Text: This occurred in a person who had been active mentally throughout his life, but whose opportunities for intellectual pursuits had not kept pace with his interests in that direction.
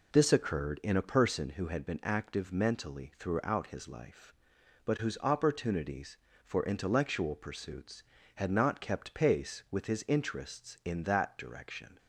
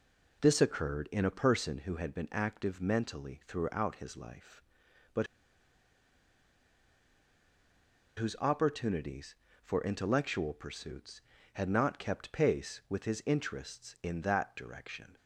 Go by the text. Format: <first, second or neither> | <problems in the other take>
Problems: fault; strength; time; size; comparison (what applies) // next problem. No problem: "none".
first | pauses between "but" and "whose"; strong; at 5.2 s; 2.9 s long